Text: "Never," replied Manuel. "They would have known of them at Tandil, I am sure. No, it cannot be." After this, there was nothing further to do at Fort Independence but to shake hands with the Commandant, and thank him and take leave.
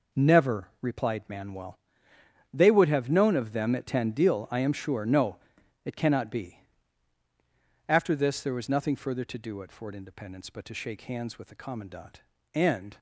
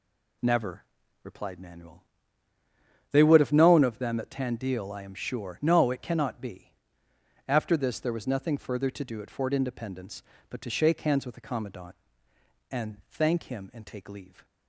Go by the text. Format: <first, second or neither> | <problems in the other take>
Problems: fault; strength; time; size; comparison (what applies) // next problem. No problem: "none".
second | stops before "thank him and take leave"; at 12.9 s